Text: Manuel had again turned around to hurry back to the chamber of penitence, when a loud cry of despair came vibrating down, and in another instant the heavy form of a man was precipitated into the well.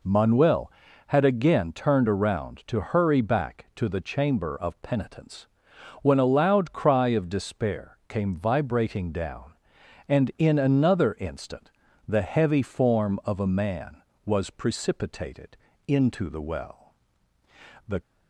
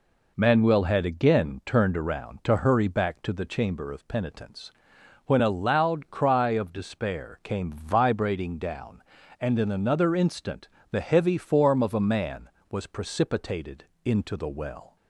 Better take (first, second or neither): second